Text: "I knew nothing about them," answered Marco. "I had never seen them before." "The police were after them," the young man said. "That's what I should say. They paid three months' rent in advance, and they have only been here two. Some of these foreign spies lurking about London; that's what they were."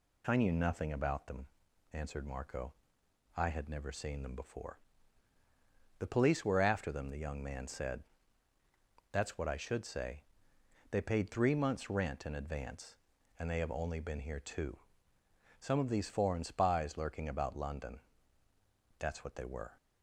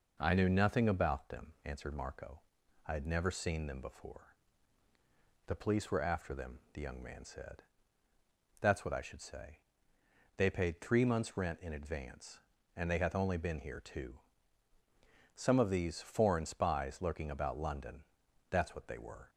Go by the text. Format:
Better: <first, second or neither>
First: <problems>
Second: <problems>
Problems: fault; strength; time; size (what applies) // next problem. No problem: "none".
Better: first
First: none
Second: says "hath" for "have"; at 12.9 s